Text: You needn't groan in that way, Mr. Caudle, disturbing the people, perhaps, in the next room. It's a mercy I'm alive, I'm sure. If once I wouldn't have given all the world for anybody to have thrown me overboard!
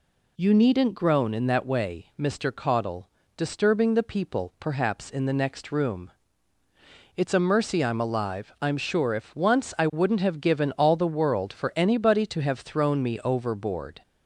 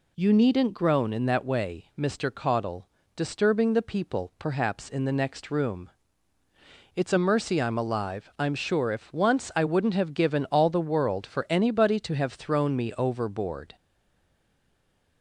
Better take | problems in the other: first | stays silent after the last word; noticeable; from 13.7 s on; 1.5 s long

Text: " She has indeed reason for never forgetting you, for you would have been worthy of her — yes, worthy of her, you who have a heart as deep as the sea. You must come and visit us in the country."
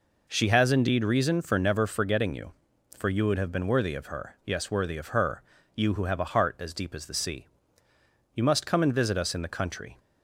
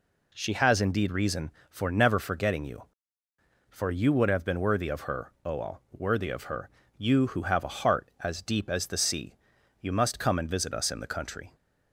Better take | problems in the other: first | says "oal" for "yes"; at 5.4 s

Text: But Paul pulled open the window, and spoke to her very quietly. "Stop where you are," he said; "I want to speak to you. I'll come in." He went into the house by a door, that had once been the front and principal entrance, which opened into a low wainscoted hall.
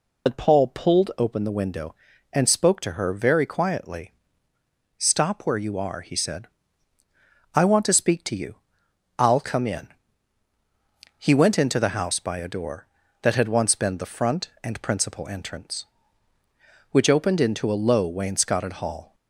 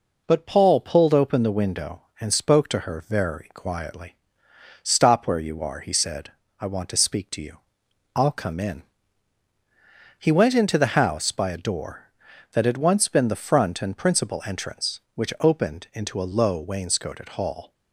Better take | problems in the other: second | loses the start of "But"; at 0.2 s; 60 ms

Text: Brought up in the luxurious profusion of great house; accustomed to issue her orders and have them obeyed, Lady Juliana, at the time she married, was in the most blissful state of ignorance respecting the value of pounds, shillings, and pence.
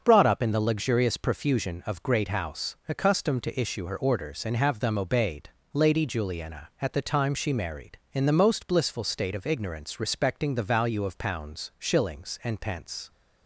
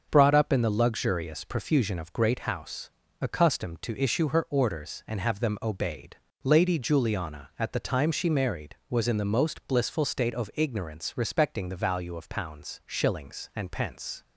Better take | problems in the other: second | starts louder than the rest; until 1.0 s; 6.5 dB; also in the second // skips "was"; at 8.0 s

